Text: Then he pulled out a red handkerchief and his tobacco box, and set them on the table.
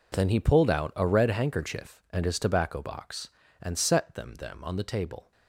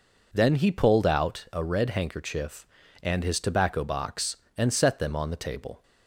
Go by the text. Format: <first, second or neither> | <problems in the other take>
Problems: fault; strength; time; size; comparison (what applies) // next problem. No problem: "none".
second | says "them" twice; at 4.3 s